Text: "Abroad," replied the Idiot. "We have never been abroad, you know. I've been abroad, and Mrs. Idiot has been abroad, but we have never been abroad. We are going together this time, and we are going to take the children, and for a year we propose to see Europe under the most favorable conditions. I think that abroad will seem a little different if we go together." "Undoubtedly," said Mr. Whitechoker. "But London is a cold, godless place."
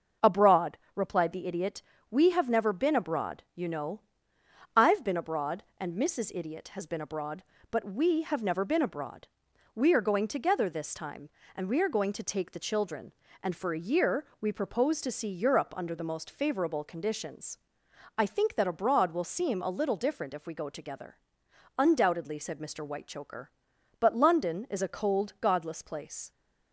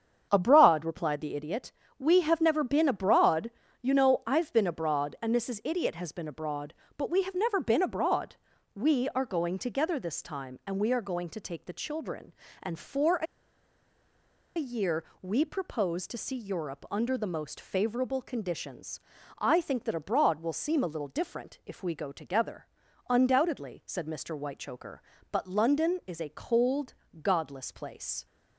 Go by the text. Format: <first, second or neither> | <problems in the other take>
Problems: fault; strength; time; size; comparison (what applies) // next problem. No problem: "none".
first | starts louder than the rest; strong; until 1.3 s; 7.5 dB; also in the first // pauses between "a" and "year"; strong; at 13.2 s; 1.3 s long // pauses between "year" and "we"; slight; at 15.0 s; 0.18 s long